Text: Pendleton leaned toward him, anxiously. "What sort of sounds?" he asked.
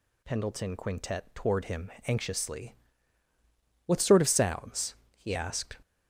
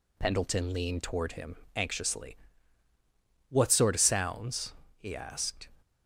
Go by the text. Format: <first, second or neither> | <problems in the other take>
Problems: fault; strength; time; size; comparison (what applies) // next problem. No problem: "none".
second | says "quintet" for "leaned"; at 0.7 s